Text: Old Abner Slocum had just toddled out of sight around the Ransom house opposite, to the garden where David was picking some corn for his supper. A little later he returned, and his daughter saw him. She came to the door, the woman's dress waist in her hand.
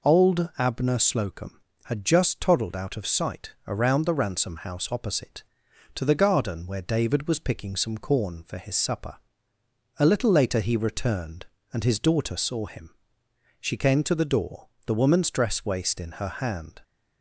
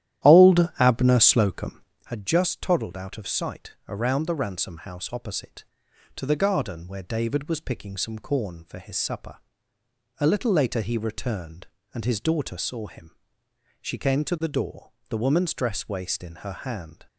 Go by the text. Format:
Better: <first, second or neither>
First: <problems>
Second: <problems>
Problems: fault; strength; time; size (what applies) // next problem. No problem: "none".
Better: first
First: none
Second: starts louder than the rest; strong; until 2.1 s; 12 dB